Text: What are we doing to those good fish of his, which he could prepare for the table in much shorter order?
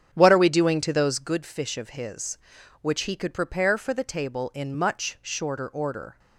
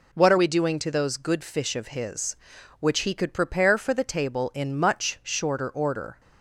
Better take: second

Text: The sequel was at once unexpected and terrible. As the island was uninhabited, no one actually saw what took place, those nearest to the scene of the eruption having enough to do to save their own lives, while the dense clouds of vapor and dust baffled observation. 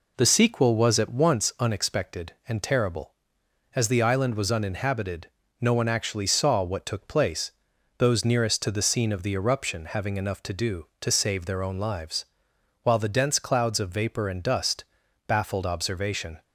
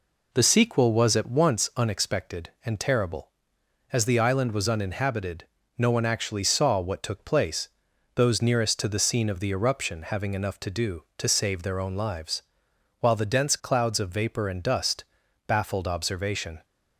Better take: neither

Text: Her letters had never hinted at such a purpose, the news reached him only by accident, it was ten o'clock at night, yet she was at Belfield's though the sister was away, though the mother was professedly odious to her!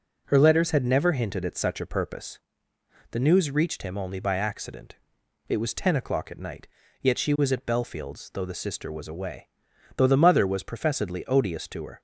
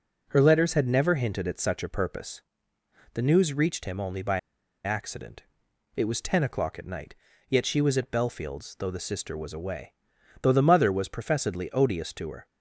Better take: first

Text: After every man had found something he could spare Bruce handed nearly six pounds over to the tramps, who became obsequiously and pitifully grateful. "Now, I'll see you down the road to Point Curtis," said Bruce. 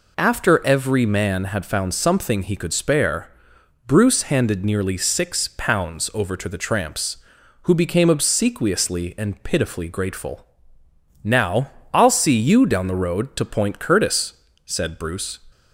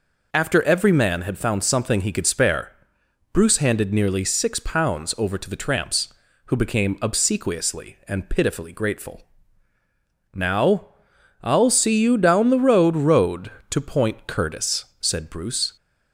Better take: first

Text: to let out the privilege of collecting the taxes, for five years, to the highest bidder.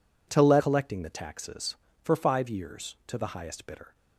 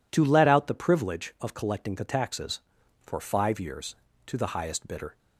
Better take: second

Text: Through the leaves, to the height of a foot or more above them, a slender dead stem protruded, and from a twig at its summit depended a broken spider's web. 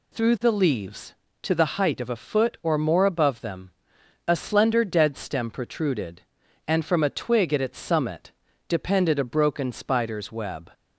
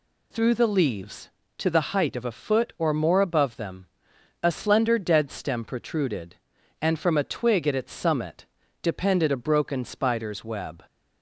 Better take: neither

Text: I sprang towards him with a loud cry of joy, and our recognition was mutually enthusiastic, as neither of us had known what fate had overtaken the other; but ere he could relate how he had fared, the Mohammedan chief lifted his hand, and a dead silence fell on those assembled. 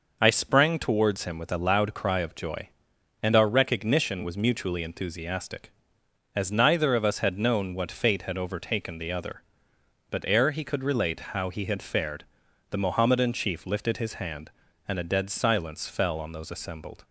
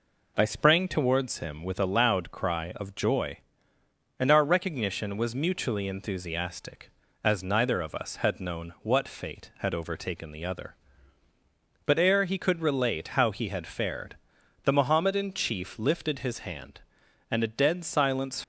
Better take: first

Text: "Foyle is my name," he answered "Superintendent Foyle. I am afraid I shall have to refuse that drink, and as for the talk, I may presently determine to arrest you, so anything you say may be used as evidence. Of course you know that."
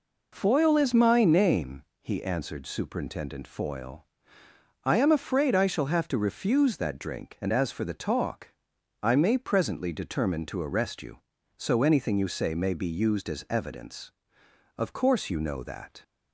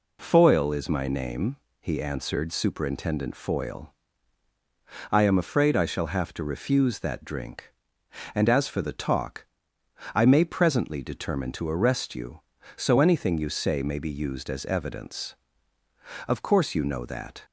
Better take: neither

